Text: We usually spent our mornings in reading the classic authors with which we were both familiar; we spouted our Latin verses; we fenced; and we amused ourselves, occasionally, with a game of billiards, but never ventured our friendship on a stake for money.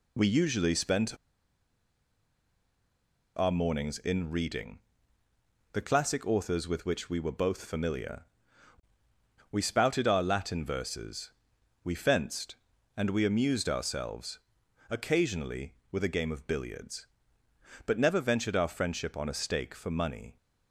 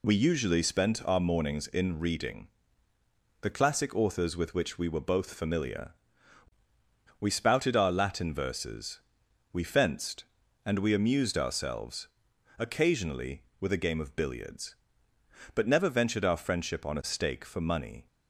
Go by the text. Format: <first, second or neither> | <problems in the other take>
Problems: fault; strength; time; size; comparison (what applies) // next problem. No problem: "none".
second | pauses between "spent" and "our"; strong; at 1.1 s; 2.2 s long // pauses between "reading" and "the"; noticeable; at 4.7 s; 0.96 s long; noticeable in the second